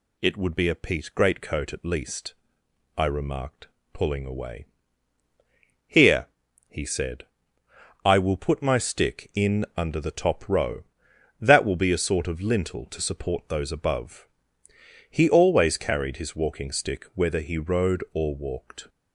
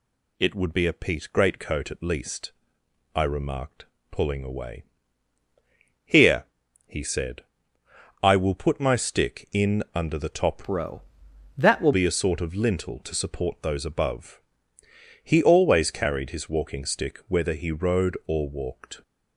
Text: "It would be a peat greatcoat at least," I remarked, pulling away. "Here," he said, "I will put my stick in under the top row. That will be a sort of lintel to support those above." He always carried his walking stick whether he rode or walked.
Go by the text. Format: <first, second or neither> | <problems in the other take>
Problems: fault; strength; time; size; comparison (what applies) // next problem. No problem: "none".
first | changes voice from "row" to "will"; from 10.6 to 11.9 s; 1.3 s long